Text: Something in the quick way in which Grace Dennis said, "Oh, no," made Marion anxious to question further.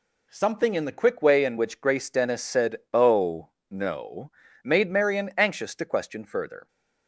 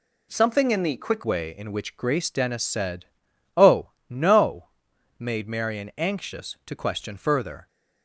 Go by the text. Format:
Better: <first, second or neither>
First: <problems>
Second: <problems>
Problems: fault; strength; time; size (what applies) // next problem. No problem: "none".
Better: first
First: none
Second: changes voice at "way"; from 1.2 s on; 6.4 s long